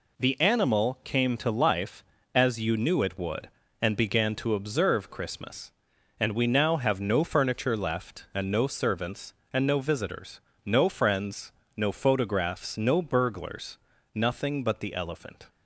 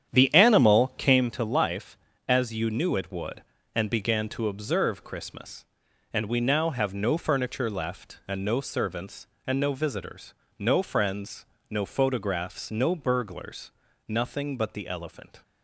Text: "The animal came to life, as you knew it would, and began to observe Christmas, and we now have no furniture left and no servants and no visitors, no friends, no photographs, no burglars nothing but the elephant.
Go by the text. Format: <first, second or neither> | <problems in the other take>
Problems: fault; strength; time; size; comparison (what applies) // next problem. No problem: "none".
first | starts louder than the rest; strong; until 1.3 s; 9 dB // pauses between "burglars" and "nothing"; at 13.7 s; 0.40 s long; also in the first